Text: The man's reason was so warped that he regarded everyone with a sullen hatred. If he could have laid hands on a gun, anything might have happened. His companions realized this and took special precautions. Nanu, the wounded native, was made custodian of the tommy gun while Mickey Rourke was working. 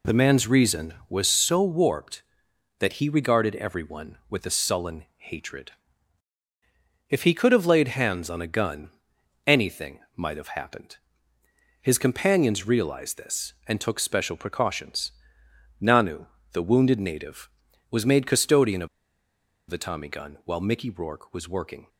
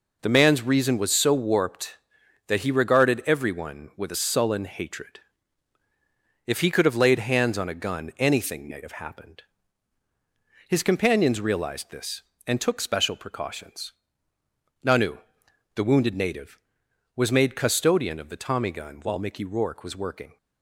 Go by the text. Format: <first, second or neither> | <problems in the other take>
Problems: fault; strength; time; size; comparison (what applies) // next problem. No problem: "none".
second | pauses between "anything" and "might"; slight; at 9.9 s; 0.18 s long // pauses between "of" and "the"; noticeable; at 18.8 s; 0.82 s long